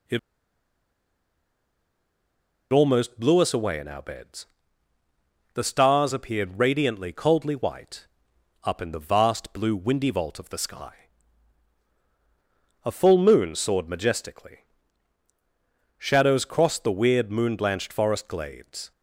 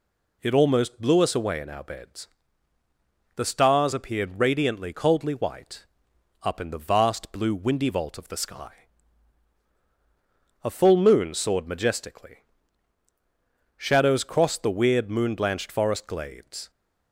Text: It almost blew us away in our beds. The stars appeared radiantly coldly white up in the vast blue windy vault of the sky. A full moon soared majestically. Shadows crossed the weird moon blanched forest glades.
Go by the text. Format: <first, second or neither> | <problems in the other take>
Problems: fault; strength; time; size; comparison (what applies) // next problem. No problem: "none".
second | pauses between "It" and "almost"; strong; at 0.1 s; 2.5 s long // pauses between "white" and "up"; noticeable; at 8.0 s; 0.56 s long; noticeable in the second